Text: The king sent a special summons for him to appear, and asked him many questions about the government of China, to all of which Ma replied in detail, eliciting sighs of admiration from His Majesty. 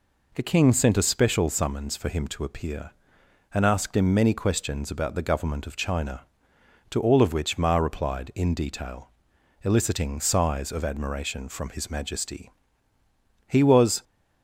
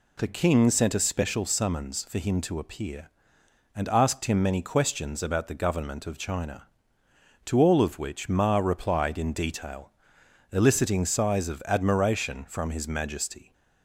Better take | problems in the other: second | goes on to say "He was"; from 13.4 s on; 0.56 s long

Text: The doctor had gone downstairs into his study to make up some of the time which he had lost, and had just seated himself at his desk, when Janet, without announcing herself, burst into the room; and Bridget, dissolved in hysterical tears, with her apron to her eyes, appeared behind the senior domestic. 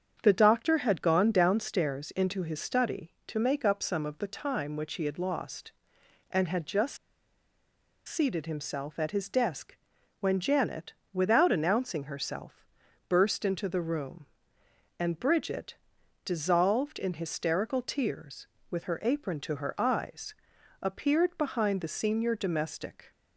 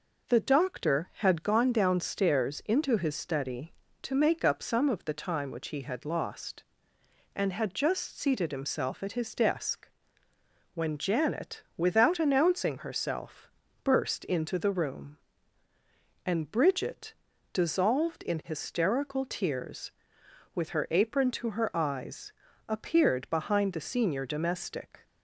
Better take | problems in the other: second | starts louder than the rest; strong; until 1.2 s; 7.5 dB // pauses between "just" and "seated"; at 6.9 s; 1.0 s long

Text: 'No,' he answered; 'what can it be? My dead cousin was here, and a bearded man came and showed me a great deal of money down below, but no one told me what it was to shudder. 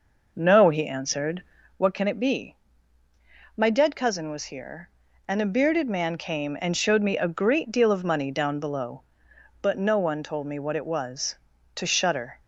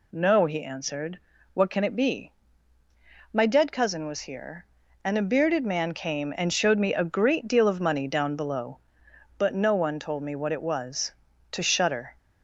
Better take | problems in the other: second | starts louder than the rest; noticeable; until 1.8 s; 5.5 dB

